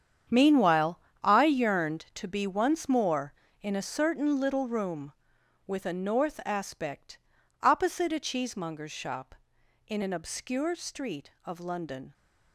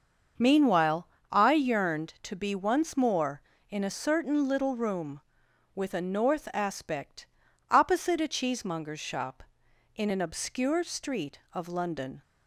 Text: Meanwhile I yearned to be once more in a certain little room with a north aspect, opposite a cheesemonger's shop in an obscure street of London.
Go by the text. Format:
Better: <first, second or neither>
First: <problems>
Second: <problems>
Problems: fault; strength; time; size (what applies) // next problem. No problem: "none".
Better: second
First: gets quieter; strong; throughout; 14 dB // starts louder than the rest; strong; until 1.5 s; 8.5 dB // pauses between "Meanwhile" and "I"; slight; at 0.9 s; 0.24 s long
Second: starts louder than the rest; until 1.6 s; 6.5 dB // pauses between "Meanwhile" and "I"; slight; at 1.0 s; 0.24 s long